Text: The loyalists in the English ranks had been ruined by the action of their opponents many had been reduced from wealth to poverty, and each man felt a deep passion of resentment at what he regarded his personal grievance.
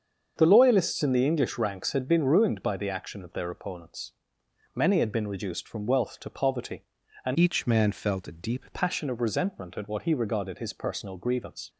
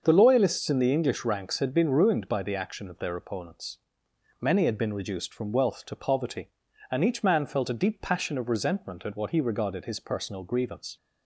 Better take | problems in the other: second | starts louder than the rest; until 1.3 s; 7 dB; also in the second // pauses between "opponents" and "many"; noticeable; at 4.1 s; 0.62 s long; noticeable in the second // changes voice from "each" to "deep"; from 7.3 to 8.6 s; 1.3 s long

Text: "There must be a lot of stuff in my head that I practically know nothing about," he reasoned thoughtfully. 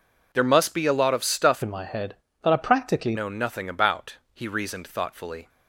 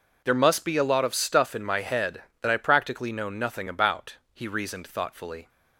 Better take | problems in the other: second | changes voice from "in" to "practically"; from 1.6 to 3.1 s; 1.5 s long

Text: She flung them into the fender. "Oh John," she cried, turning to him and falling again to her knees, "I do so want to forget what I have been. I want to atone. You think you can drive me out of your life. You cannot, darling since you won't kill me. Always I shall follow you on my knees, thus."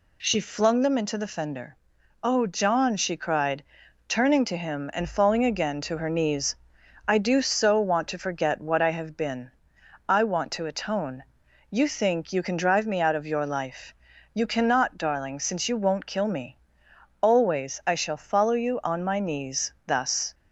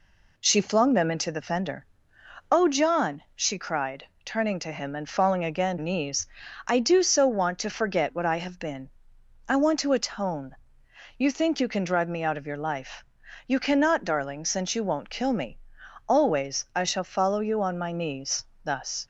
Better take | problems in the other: first | skips "to her"; at 5.7 s

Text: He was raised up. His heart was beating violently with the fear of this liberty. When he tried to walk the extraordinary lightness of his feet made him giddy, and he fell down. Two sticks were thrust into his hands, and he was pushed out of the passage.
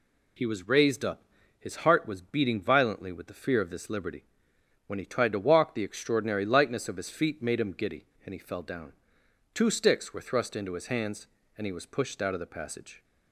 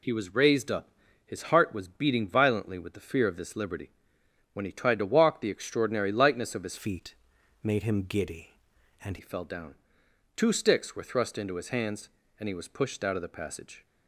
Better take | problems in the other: first | changes voice from "feet" to "and"; from 6.7 to 9.1 s; 2.4 s long // pauses between "feet" and "made"; noticeable; at 7.1 s; 0.48 s long

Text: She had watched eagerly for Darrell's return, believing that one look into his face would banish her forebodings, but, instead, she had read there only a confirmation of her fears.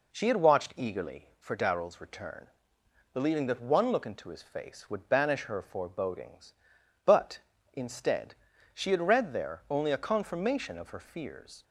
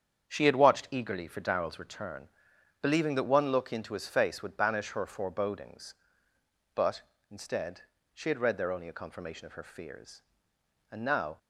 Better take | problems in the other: first | starts louder than the rest; strong; until 1.3 s; 8 dB // goes on to say "And now"; slight; from 10.8 s on; 0.48 s long

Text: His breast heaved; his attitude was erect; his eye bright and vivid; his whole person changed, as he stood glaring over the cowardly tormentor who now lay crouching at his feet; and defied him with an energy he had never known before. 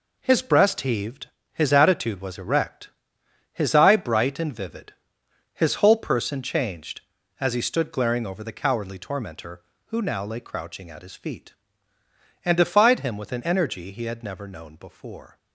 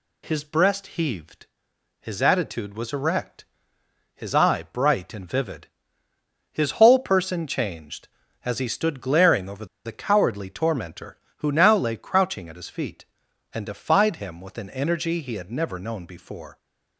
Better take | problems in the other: first | pauses between "over" and "the"; slight; at 9.6 s; 0.18 s long

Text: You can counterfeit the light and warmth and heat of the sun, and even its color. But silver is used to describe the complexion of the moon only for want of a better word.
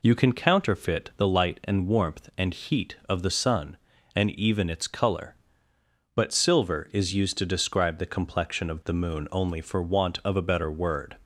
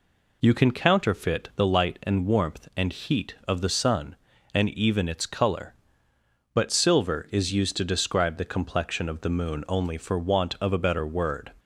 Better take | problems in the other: neither | none

